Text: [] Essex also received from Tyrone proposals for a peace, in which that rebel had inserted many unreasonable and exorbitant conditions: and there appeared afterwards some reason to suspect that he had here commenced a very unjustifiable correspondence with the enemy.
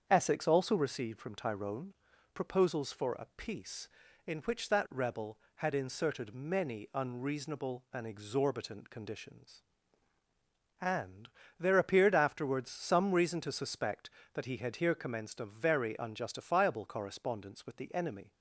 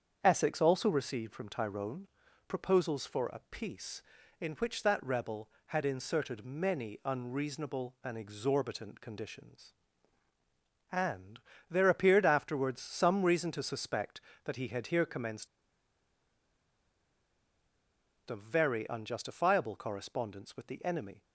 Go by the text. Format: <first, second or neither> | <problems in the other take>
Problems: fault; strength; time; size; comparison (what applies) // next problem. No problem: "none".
first | starts louder than the rest; strong; until 1.2 s; 7.5 dB; strong in the first // pauses between "Tyrone" and "proposals"; at 2.0 s; 0.42 s long; also in the first // pauses between "and" and "there"; slight; at 11.4 s; 0.30 s long; slight in the first // pauses between "commenced" and "a"; strong; at 15.4 s; 2.8 s long